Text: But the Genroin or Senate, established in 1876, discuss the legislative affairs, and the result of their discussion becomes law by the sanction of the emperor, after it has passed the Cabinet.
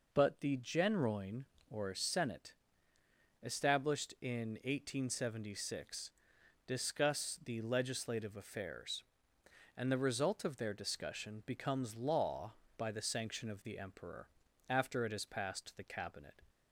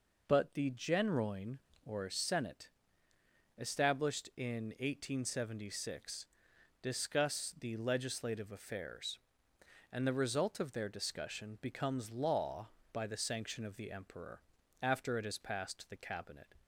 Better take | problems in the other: neither | none

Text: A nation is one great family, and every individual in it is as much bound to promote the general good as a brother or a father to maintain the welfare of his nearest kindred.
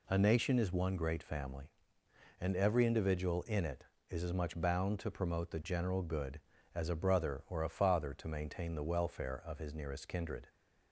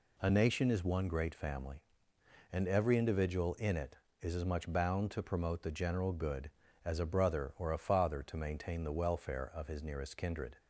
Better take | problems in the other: neither | none

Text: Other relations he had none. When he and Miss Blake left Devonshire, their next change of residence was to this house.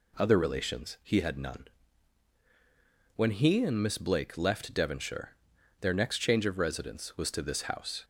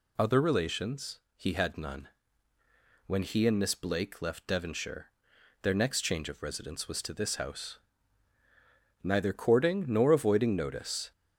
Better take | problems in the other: first | pauses between "relations" and "he"; slight; at 1.1 s; 0.16 s long // goes on to say "Neither courting nor avoiding notice"; strong; from 9.0 s on; 2.0 s long

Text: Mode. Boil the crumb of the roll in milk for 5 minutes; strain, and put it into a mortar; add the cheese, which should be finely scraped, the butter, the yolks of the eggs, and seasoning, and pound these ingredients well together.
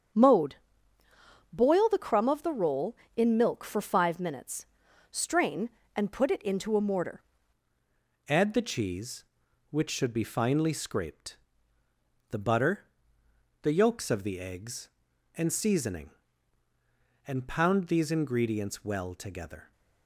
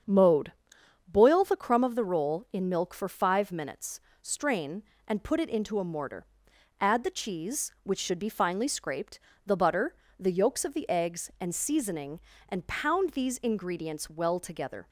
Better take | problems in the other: second | starts louder than the rest; strong; until 2.0 s; 7.5 dB; strong in the second // changes voice at "add"; from 8.2 s on; 11.5 s long

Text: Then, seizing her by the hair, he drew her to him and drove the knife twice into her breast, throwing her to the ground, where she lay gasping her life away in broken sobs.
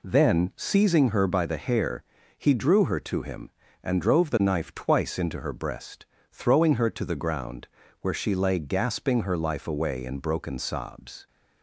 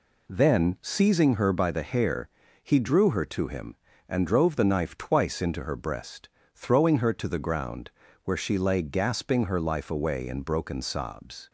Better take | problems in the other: neither | none

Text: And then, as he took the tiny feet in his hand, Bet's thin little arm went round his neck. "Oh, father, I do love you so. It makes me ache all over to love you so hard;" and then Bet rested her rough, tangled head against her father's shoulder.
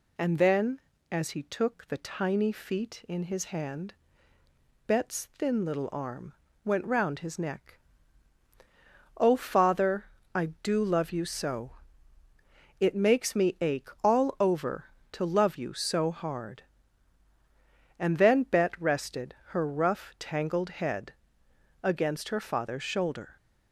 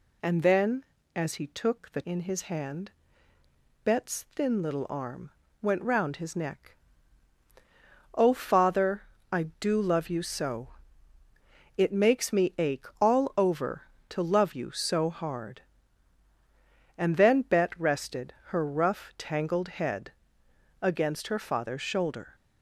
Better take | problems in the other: first | skips "tiny feet"; at 2.0 s // pauses between "arm" and "went"; slight; at 5.3 s; 0.30 s long; slight in the first // pauses between "ache" and "all"; slight; at 12.8 s; 0.16 s long; slight in the first // pauses between "head" and "against"; noticeable; at 20.1 s; 0.68 s long; noticeable in the first

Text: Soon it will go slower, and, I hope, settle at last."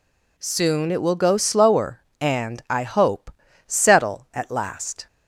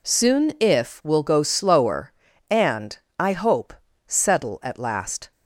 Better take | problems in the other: first | says "if" for "it"; at 0.5 s

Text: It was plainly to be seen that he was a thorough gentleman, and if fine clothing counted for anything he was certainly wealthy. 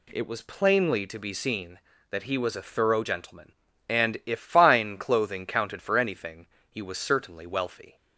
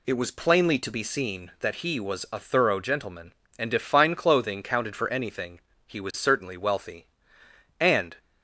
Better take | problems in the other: first | pauses between "anything" and "he"; slight; at 5.5 s; 0.28 s long; slight in the first // goes on to say "And"; slight; from 7.7 s on; 0.36 s long

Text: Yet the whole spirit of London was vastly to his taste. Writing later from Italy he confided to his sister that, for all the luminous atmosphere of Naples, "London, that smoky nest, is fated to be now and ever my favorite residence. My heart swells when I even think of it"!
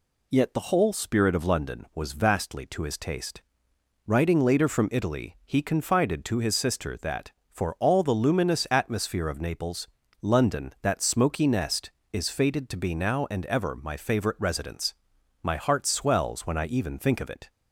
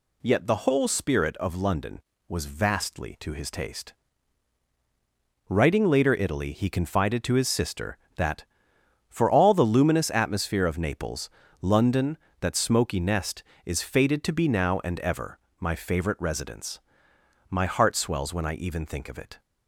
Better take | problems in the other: first | skips "from"; at 6.1 s // pauses between "ever" and "my"; slight; at 15.3 s; 0.22 s long

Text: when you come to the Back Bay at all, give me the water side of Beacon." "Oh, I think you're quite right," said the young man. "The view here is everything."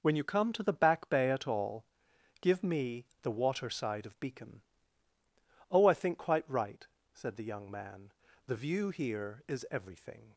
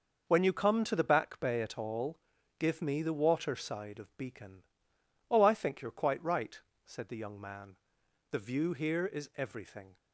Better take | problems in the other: second | pauses between "me" and "the"; slight; at 3.0 s; 0.18 s long // skips "you're"; at 6.1 s

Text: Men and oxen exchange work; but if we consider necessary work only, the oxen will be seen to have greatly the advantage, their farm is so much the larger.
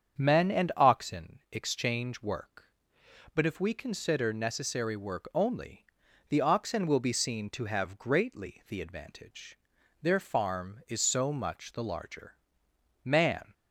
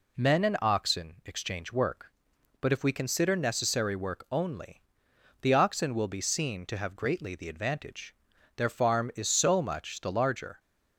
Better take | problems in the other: second | starts louder than the rest; strong; until 1.2 s; 7.5 dB // goes on to say "Man"; slight; from 13.0 s on; 0.48 s long

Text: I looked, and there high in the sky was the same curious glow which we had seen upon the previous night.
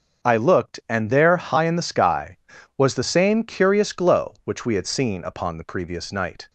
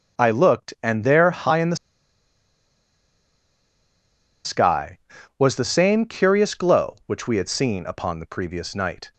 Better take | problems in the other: first | starts louder than the rest; until 1.2 s; 7 dB; also in the first // pauses between "the" and "sky"; strong; at 1.7 s; 2.6 s long

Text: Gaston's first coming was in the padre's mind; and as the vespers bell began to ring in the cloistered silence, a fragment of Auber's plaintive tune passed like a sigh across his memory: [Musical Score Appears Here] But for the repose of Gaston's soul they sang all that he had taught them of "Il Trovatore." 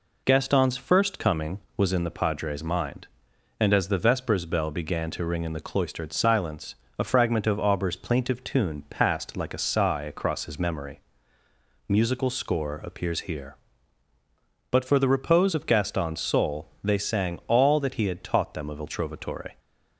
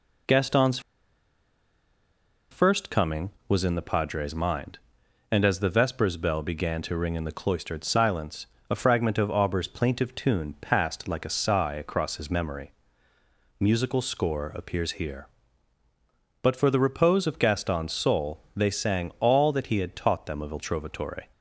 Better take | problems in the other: first | pauses between "Gaston's" and "first"; strong; at 0.7 s; 1.7 s long // pauses between "soul" and "they"; slight; at 18.4 s; 0.16 s long; slight in the first

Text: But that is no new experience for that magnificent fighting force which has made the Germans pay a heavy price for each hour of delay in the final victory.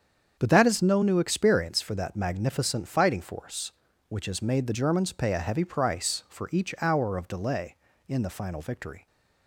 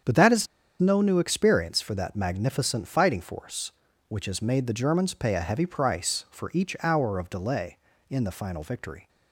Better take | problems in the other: first | starts louder than the rest; strong; until 1.3 s; 7.5 dB; strong in the first // pauses between "is" and "no"; slight; at 0.4 s; 0.33 s long

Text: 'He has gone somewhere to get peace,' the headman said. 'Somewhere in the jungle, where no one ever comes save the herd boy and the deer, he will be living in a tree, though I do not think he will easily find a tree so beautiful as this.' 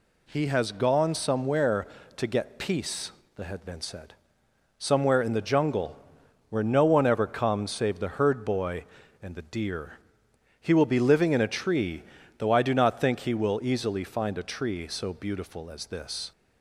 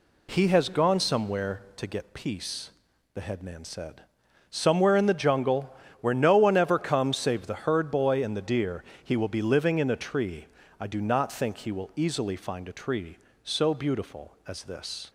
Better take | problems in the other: first | skips "though"; at 10.6 s

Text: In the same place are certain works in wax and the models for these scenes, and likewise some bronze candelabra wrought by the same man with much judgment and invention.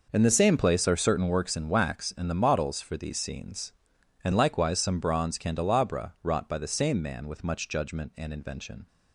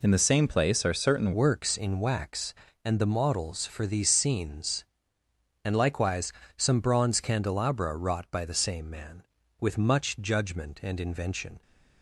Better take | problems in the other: first | changes voice at "works"; from 1.3 s on; 10.3 s long // pauses between "likewise" and "some"; slight; at 6.3 s; 0.24 s long

